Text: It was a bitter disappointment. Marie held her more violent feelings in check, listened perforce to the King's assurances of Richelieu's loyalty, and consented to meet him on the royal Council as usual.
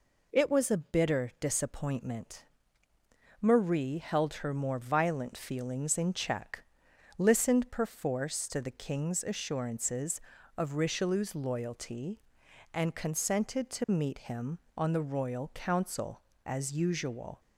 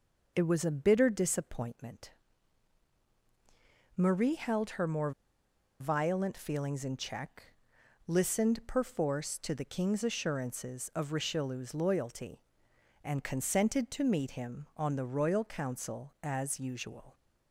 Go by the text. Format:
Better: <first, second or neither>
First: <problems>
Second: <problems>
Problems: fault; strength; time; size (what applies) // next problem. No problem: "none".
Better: first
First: none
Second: pauses between "more" and "violent"; noticeable; at 5.1 s; 0.68 s long